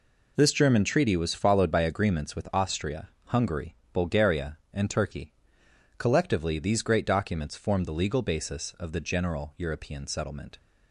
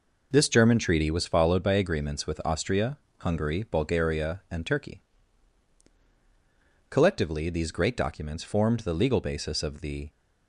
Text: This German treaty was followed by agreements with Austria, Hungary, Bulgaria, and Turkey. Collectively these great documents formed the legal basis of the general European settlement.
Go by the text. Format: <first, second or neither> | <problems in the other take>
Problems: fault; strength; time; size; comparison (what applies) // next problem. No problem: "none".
first | stops before "general European settlement"; at 10.0 s